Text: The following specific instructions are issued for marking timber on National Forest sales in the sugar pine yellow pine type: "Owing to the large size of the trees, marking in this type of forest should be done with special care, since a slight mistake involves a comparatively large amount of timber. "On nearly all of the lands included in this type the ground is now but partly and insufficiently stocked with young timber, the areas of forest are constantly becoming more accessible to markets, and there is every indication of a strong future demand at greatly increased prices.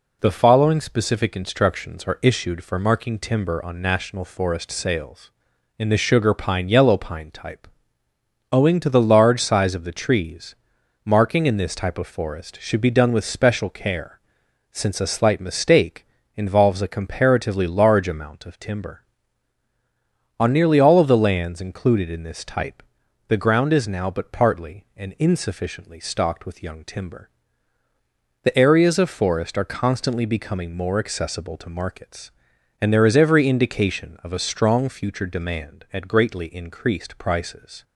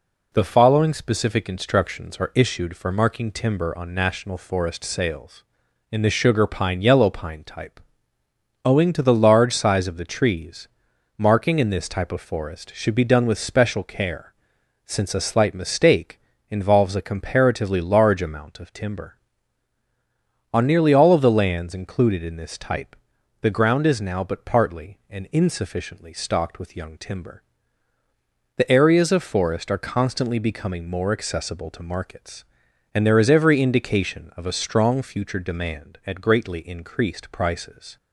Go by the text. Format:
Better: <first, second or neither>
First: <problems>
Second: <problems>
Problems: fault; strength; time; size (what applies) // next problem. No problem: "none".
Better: neither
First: pauses between "mistake" and "involves"; slight; at 16.0 s; 0.30 s long // pauses between "type" and "the"; noticeable; at 22.8 s; 0.46 s long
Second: pauses between "mistake" and "involves"; slight; at 16.1 s; 0.30 s long // pauses between "type" and "the"; noticeable; at 22.9 s; 0.46 s long